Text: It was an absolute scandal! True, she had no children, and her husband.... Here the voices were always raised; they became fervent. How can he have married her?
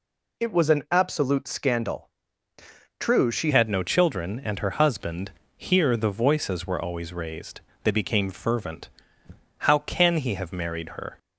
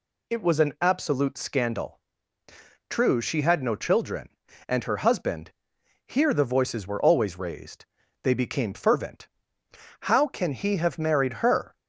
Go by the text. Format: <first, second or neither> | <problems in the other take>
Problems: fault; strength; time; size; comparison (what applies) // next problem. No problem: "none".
second | changes voice at "had"; from 3.5 s on; 7.6 s long